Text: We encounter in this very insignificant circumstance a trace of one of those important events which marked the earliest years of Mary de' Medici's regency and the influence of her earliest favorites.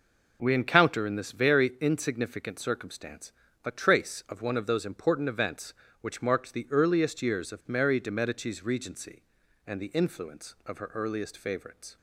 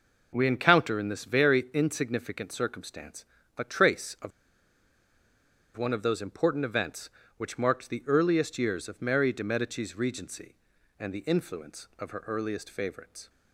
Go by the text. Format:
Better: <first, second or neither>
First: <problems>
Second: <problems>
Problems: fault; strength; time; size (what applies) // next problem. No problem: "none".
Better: first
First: pauses between "circumstance" and "a"; slight; at 3.3 s; 0.32 s long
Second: pauses between "circumstance" and "a"; slight; at 3.2 s; 0.32 s long // pauses between "of" and "one"; strong; at 4.3 s; 1.4 s long